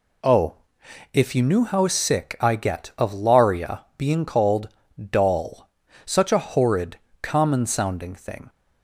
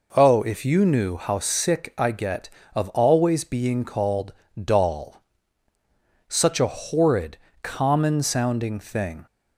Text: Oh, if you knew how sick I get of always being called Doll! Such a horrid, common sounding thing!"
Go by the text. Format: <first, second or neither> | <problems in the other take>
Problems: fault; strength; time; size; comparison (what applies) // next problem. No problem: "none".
second | says "laria" for "always"; at 3.1 s // pauses between "called" and "Doll"; slight; at 4.6 s; 0.32 s long; slight in the second